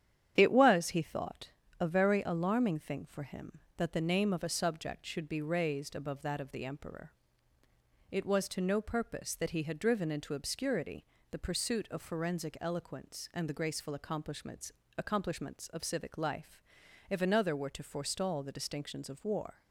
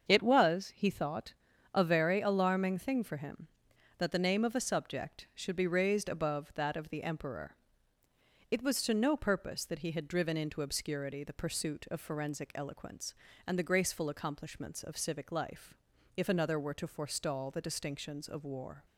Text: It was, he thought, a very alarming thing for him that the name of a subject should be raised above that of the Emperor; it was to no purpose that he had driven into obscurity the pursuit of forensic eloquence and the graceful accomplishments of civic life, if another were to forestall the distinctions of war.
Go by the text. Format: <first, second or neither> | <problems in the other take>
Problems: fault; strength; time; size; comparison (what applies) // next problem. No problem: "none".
second | starts louder than the rest; strong; until 1.3 s; 9 dB; also in the second // pauses between "obscurity" and "the"; slight; at 11.0 s; 0.24 s long // says "accomplishments" twice; at 14.9 s